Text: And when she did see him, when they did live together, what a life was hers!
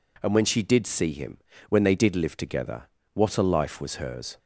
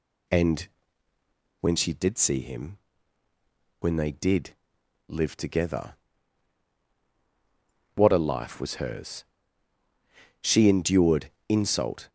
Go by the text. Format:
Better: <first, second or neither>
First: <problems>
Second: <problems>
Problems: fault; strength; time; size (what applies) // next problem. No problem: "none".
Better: first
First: none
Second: pauses between "And" and "when"; noticeable; at 0.6 s; 0.92 s long // pauses between "did" and "live"; noticeable; at 4.5 s; 0.56 s long // goes on to say "She endured insult"; strong; from 10.4 s on; 1.6 s long